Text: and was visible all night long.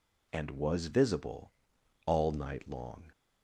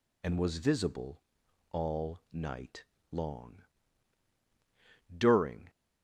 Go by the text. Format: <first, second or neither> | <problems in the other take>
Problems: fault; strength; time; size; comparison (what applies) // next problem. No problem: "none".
first | pauses between "visible" and "all"; noticeable; at 1.2 s; 0.52 s long; noticeable in the first // pauses between "night" and "long"; slight; at 2.8 s; 0.28 s long // goes on to say "During"; from 5.1 s on; 0.54 s long